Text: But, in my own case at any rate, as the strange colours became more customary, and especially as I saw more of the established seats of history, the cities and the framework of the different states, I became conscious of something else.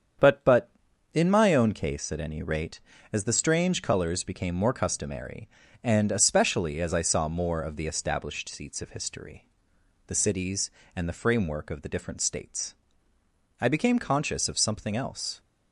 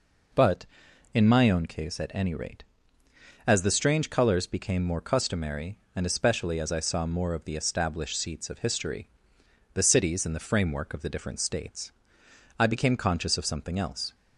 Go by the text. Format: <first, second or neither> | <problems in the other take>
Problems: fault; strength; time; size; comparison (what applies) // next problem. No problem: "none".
second | starts louder than the rest; strong; until 1.6 s; 8 dB // says "But" twice; at 0.4 s